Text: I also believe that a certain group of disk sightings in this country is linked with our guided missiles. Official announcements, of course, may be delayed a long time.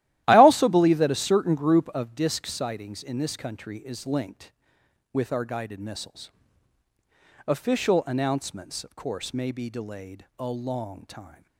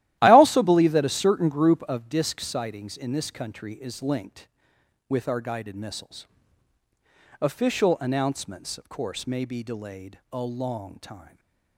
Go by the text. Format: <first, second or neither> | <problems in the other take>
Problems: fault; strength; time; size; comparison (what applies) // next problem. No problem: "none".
neither | starts louder than the rest; strong; the same in both